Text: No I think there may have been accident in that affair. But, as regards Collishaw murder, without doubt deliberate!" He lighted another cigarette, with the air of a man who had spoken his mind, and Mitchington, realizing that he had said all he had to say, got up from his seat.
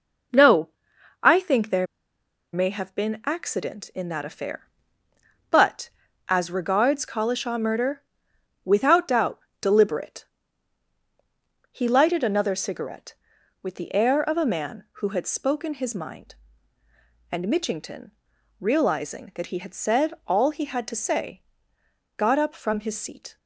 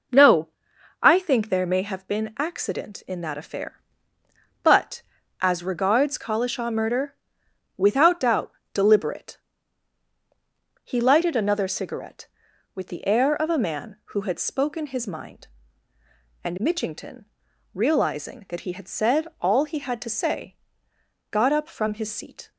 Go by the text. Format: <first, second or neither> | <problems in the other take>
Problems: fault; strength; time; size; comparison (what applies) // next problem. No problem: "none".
second | pauses between "No" and "I"; noticeable; at 0.6 s; 0.52 s long; noticeable in the second // pauses between "there" and "may"; noticeable; at 1.8 s; 0.67 s long // pauses between "doubt" and "deliberate"; slight; at 9.3 s; 0.22 s long; slight in the second